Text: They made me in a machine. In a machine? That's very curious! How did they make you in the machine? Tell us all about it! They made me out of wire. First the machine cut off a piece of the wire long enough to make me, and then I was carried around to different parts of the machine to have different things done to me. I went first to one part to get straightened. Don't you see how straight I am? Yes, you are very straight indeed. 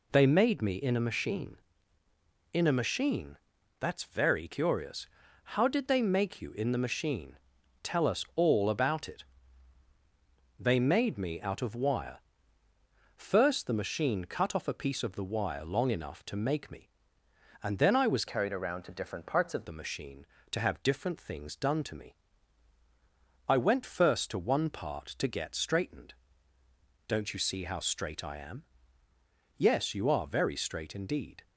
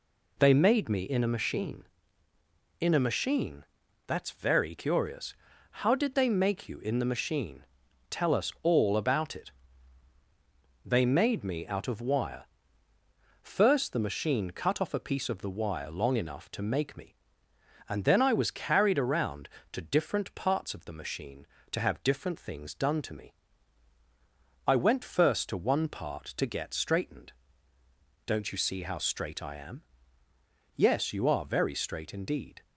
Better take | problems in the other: second | changes voice from "carried" to "of"; from 18.2 to 19.6 s; 1.4 s long

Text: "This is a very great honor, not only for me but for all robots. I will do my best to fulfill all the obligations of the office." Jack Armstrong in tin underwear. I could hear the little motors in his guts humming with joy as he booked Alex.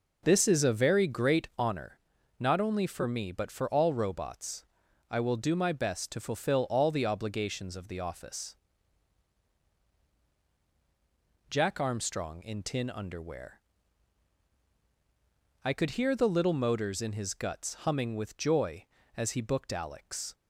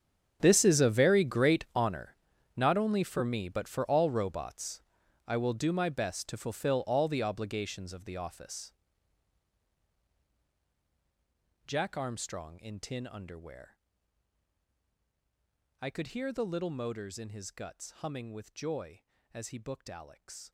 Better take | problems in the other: first | gets quieter; strong; throughout; 17.5 dB

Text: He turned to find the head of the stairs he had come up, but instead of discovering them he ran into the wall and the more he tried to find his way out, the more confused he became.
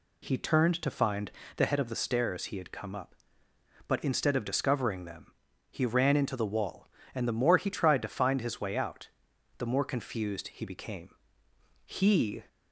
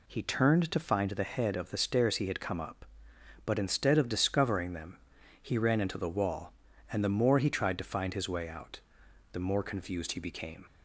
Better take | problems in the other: second | pauses between "find" and "the"; slight; at 1.2 s; 0.28 s long // pauses between "them" and "he"; slight; at 5.3 s; 0.36 s long; also in the second // goes on to say "He"; from 11.8 s on; 0.60 s long

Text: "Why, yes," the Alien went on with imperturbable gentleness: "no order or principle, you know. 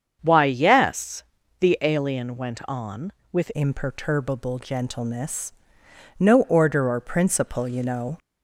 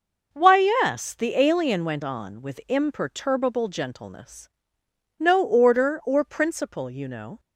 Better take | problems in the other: second | starts louder than the rest; strong; until 1.2 s; 7 dB // changes voice at "imperturbable"; from 3.5 s on; 4.6 s long

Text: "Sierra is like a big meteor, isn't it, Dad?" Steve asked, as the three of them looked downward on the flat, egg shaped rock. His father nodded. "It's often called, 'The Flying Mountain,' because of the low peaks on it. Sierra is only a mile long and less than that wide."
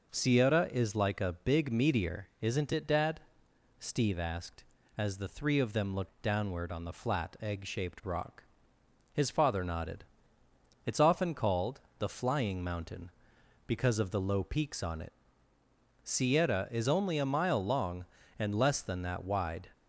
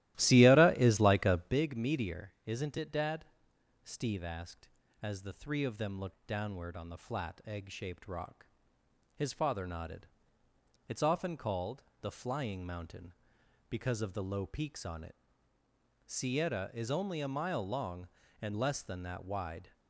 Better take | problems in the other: first | starts louder than the rest; strong; until 1.7 s; 15.5 dB

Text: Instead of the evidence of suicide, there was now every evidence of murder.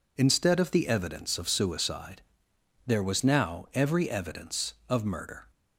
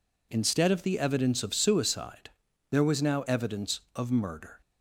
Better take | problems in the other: first | skips "every"; at 3.2 s

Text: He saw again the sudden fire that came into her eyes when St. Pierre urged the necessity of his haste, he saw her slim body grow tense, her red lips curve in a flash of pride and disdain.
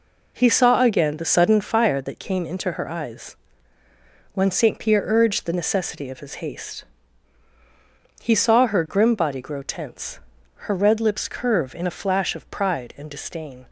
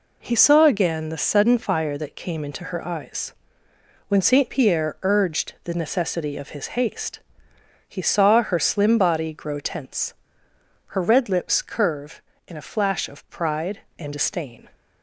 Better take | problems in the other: second | pauses between "eyes" and "when"; noticeable; at 3.3 s; 0.96 s long; noticeable in the second // says "grim" for "slim"; at 8.8 s

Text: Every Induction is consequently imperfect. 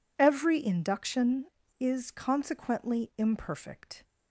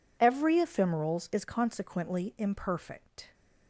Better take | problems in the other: first | says "Ephemerals" for "Induction"; at 0.5 s

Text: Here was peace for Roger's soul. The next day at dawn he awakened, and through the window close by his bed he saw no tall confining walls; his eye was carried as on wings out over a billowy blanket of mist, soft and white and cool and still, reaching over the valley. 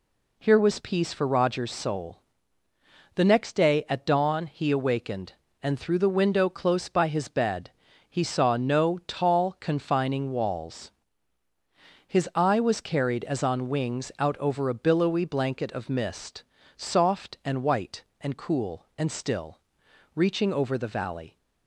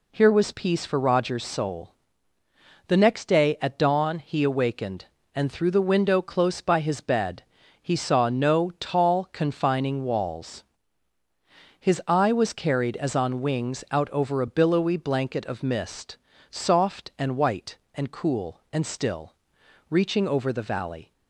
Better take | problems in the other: neither | pauses between "bed" and "he"; slight; the same in both

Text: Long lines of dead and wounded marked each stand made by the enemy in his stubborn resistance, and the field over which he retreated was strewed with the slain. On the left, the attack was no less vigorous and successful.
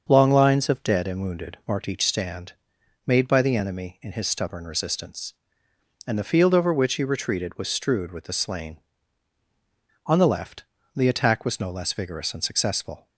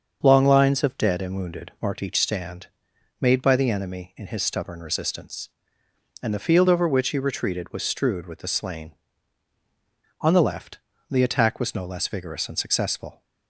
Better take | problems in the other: neither | starts louder than the rest; the same in both // pauses between "stand" and "made"; noticeable; the same in both

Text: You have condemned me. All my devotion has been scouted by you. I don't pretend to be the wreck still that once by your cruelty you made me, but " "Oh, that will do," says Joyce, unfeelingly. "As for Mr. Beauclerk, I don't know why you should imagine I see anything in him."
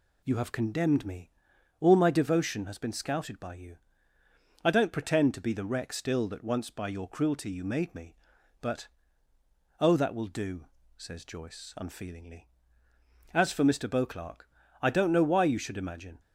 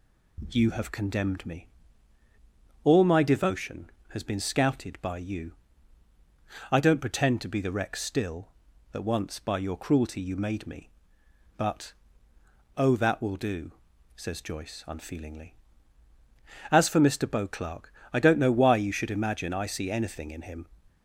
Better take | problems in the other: second | stops before "I see anything in him"; at 16.1 s

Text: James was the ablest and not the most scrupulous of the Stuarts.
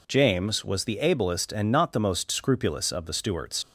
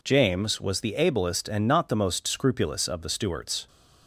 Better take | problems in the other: second | leaves "Stuarts" unfinished; at 3.6 s; 80 ms

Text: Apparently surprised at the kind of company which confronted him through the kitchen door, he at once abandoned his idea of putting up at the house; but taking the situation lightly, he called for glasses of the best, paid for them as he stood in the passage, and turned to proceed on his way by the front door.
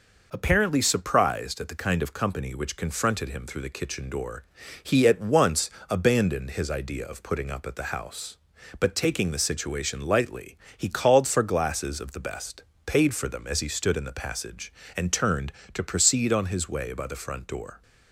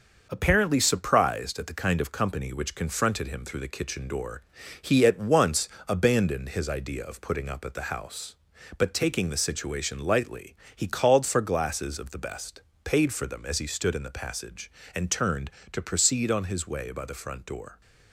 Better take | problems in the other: first | gets quieter; noticeable; throughout; 4.5 dB // pauses between "once" and "abandoned"; slight; at 5.6 s; 0.18 s long; slight in the first

